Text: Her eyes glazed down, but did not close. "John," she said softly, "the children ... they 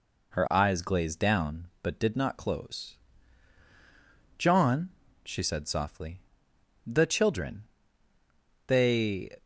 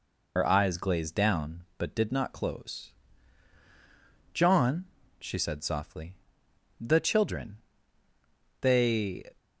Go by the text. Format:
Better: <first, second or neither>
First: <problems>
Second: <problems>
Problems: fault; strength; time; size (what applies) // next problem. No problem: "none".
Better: first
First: none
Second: loses the start of "Her"; at 0.3 s; 60 ms